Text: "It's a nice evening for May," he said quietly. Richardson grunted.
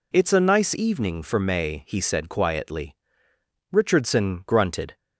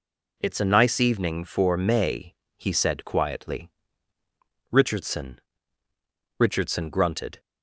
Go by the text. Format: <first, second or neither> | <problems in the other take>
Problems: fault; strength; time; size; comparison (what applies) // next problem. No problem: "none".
first | says "Richardson" twice; at 6.3 s